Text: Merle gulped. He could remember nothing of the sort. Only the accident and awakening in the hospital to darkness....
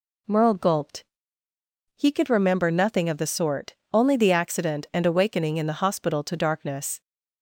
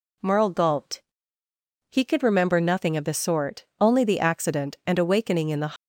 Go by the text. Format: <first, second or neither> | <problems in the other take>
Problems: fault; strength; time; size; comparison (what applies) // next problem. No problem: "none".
first | stops before "hospital to darkness"; at 5.7 s